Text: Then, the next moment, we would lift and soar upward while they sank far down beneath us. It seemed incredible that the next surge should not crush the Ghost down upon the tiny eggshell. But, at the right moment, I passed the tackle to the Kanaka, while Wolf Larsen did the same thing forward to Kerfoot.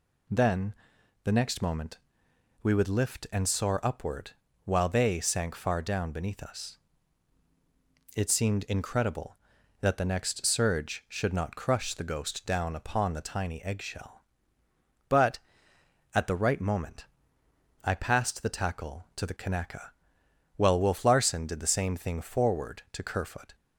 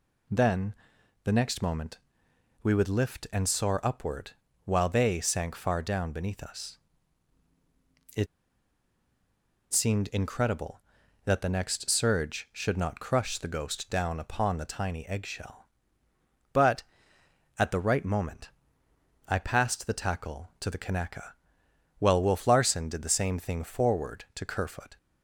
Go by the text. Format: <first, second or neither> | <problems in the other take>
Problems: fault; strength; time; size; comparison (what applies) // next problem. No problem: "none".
first | pauses between "upward" and "while"; slight; at 4.3 s; 0.34 s long; slight in the first // pauses between "It" and "seemed"; strong; at 8.2 s; 1.4 s long